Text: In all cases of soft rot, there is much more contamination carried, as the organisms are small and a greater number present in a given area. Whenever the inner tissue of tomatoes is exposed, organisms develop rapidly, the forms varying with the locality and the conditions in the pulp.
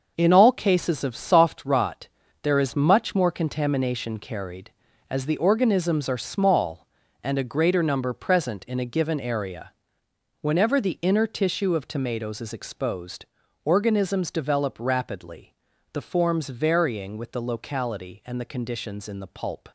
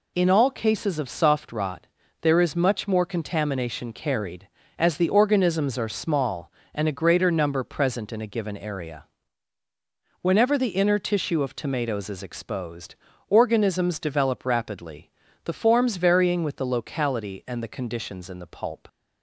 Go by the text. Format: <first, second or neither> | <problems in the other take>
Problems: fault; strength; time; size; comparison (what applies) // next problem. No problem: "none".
second | gets quieter; strong; throughout; 8.5 dB